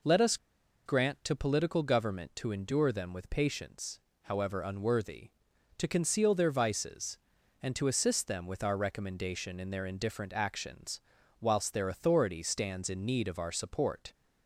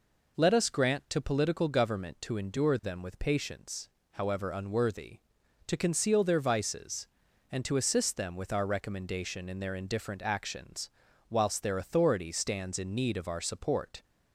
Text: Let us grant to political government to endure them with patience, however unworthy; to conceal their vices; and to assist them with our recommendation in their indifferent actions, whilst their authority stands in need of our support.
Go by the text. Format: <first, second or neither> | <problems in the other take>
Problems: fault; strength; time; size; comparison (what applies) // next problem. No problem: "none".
second | pauses between "us" and "grant"; noticeable; at 0.3 s; 0.49 s long